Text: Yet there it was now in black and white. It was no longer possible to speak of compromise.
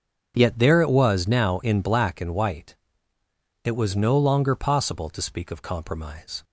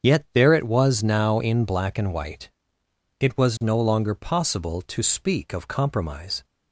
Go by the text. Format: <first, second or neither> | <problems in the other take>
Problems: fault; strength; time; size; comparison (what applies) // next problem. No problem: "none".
neither | starts louder than the rest; strong; the same in both